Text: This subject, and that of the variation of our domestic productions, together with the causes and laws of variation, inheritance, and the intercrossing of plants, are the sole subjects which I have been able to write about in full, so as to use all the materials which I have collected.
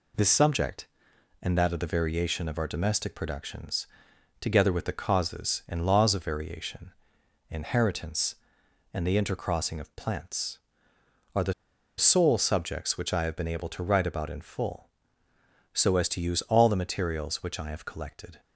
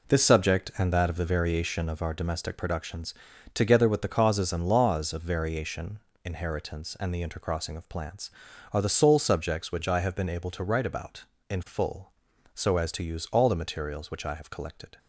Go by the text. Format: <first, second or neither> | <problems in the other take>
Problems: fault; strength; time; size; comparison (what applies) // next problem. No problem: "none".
second | pauses between "the" and "sole"; at 11.5 s; 0.44 s long